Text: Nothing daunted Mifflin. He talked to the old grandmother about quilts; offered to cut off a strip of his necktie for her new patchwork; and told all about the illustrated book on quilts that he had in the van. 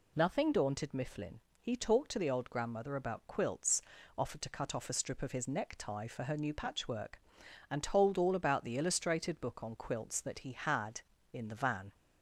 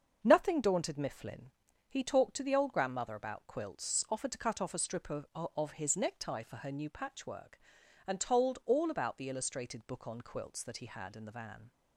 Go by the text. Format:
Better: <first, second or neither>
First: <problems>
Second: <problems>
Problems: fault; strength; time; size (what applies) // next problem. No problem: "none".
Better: first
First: none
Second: starts louder than the rest; until 1.2 s; 6.5 dB // says "of" twice; at 5.3 s